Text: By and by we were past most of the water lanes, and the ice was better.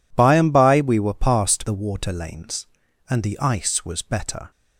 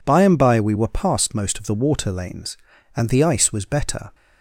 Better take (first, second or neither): second